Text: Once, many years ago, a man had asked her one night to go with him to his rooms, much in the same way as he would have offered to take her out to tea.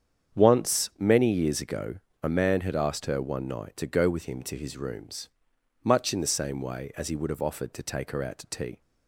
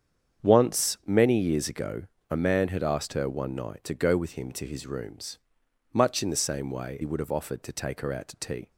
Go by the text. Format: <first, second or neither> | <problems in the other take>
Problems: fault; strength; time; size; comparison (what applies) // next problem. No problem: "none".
first | starts louder than the rest; strong; until 1.5 s; 8 dB; strong in the first // skips "as"; at 6.9 s